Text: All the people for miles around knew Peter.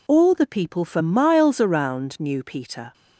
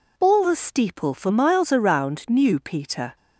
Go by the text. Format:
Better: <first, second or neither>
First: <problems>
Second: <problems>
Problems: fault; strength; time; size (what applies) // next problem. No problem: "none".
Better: first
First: none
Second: says "steeple" for "people"; at 0.5 s